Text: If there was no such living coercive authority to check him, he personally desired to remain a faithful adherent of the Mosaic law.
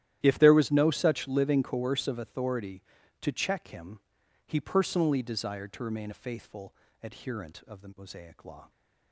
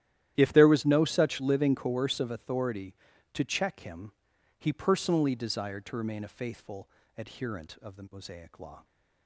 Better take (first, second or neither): neither